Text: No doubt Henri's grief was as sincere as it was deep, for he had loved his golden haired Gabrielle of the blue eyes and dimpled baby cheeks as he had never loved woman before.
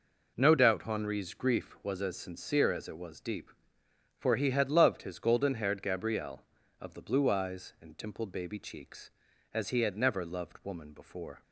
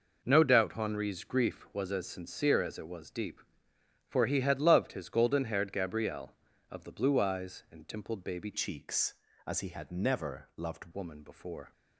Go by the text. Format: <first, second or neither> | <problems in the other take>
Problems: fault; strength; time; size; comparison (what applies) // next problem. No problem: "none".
first | changes voice from "cheeks" to "loved"; from 8.5 to 10.9 s; 2.4 s long